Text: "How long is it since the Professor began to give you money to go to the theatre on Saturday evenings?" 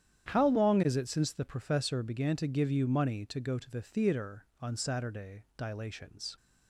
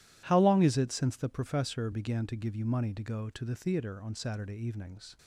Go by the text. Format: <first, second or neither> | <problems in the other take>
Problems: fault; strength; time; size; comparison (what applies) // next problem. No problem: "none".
second | starts louder than the rest; strong; until 1.3 s; 10 dB // says "dilations" for "evenings"; at 5.5 s